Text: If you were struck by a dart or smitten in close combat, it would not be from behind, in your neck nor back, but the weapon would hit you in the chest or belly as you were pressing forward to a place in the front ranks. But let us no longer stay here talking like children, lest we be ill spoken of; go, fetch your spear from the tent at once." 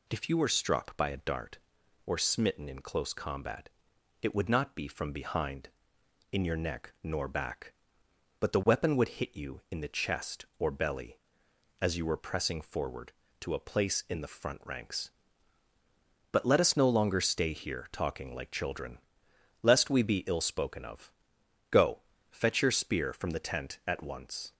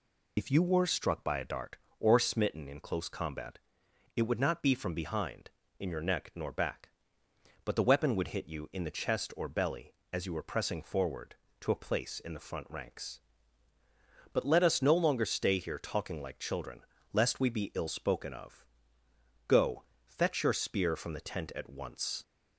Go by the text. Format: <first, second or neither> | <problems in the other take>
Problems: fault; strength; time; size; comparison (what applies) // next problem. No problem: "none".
first | loses the start of "If"; at 0.3 s; 65 ms